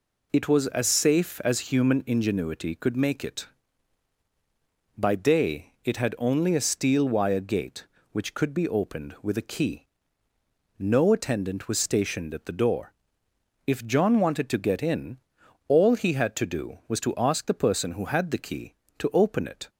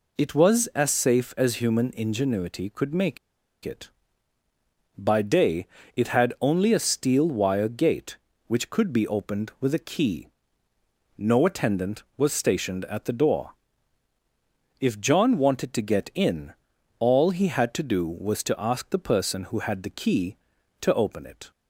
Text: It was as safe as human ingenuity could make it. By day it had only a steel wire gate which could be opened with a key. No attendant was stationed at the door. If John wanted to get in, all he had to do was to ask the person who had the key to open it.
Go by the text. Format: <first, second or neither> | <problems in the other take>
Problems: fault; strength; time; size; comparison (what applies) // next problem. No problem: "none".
first | pauses between "make" and "it"; noticeable; at 3.1 s; 0.46 s long // pauses between "day" and "it"; slight; at 5.6 s; 0.30 s long